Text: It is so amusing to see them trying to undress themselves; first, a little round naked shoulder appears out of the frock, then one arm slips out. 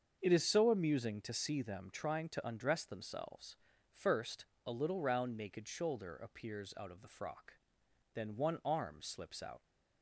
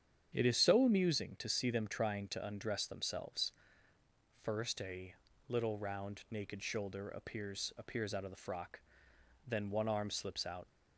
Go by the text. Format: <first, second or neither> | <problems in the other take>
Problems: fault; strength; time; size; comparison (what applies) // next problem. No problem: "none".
first | starts louder than the rest; strong; until 1.3 s; 8 dB; also in the first // pauses between "a" and "little"; slight; at 5.1 s; 0.34 s long // says "appears" twice; at 7.7 s